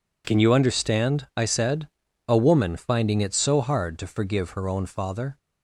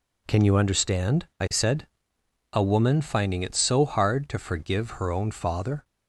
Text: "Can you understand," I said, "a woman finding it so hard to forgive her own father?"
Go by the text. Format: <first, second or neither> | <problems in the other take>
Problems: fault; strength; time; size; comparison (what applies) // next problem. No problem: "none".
neither | none